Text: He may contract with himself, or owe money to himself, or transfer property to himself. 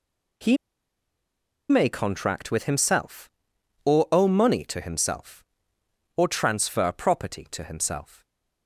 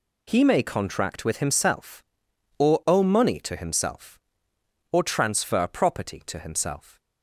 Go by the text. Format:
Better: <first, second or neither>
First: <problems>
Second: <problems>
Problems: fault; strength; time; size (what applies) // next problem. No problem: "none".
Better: second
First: pauses between "He" and "may"; at 0.5 s; 1.1 s long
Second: none